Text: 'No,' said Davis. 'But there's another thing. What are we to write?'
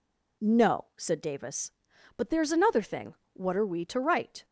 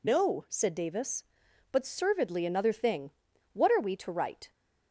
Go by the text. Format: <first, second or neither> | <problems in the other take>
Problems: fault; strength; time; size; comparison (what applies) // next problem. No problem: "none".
first | says "servedly" for "there's"; at 1.8 s